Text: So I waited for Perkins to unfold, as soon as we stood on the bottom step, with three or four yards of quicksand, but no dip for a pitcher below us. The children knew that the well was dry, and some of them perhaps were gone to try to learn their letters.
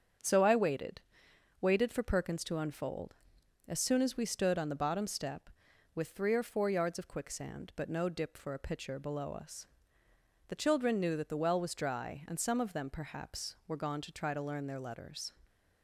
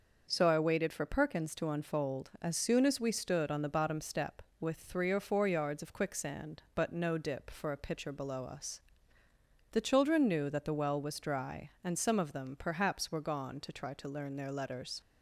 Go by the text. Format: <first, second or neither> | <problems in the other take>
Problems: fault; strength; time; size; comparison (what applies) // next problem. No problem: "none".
second | starts louder than the rest; strong; until 1.8 s; 7.5 dB; also in the second // says "waited" twice; at 1.5 s